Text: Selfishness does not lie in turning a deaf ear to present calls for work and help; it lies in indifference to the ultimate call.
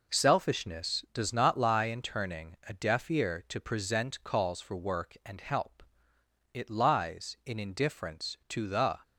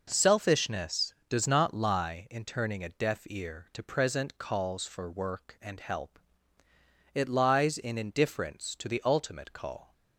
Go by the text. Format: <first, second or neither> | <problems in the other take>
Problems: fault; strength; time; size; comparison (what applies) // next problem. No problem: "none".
second | stops before "ultimate call"; at 9.0 s